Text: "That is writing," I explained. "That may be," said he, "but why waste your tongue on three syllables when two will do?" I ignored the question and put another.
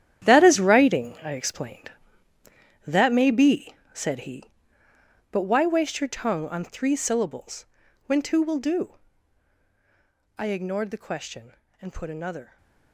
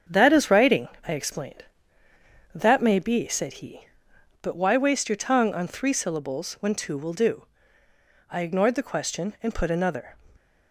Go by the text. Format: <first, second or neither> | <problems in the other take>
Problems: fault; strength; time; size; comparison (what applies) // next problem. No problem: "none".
second | gets quieter; strong; throughout; 12 dB // starts louder than the rest; strong; until 1.3 s; 10.5 dB; strong in the second // pauses between "syllables" and "when"; at 7.6 s; 0.42 s long